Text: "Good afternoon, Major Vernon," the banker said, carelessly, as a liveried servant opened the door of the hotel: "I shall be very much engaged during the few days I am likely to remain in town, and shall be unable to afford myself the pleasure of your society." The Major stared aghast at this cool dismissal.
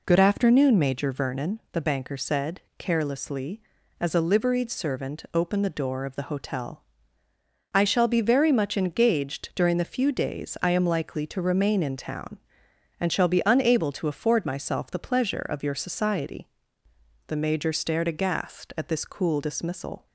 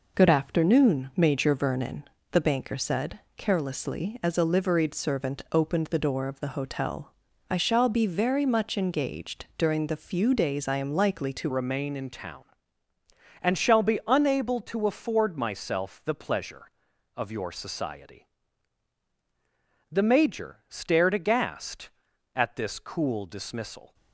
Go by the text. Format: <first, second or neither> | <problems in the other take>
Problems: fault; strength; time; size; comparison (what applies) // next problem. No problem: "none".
first | changes voice at "remain"; from 11.4 s on; 12.5 s long